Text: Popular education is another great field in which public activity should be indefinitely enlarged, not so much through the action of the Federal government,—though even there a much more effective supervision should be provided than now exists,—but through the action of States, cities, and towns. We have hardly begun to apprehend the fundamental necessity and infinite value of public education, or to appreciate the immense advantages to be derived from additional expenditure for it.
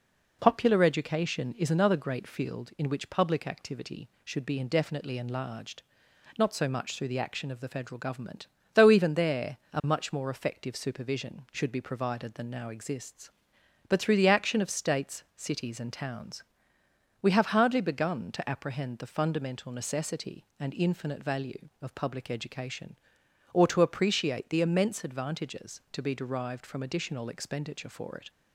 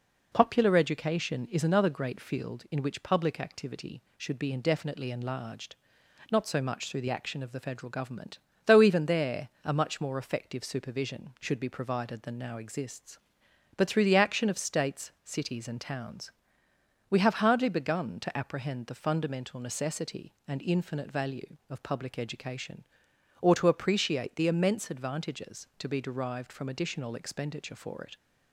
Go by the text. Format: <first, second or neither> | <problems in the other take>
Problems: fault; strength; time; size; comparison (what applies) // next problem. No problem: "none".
neither | pauses between "there" and "a"; slight; the same in both